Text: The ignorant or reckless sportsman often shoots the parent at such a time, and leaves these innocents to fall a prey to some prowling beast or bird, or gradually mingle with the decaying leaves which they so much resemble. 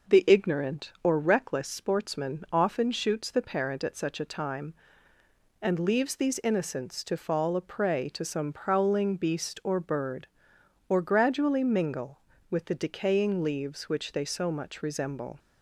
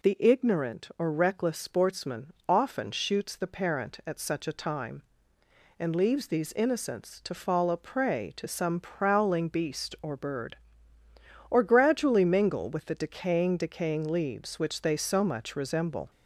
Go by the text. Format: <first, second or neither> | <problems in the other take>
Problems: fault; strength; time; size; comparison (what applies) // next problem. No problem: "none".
first | pauses between "sportsman" and "often"; slight; at 2.2 s; 0.20 s long // says "decaying" twice; at 13.5 s